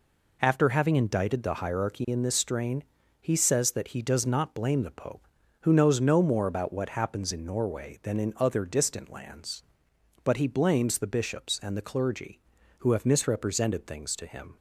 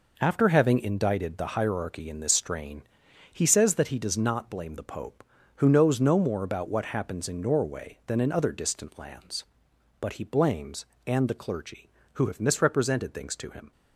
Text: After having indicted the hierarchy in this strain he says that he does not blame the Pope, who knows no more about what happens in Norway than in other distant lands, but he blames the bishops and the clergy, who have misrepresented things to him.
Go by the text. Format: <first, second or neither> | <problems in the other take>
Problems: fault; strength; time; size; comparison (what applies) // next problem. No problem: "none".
first | pauses between "strain" and "he"; noticeable; at 2.8 s; 0.48 s long; also in the first // skips "the bishops"; at 10.9 s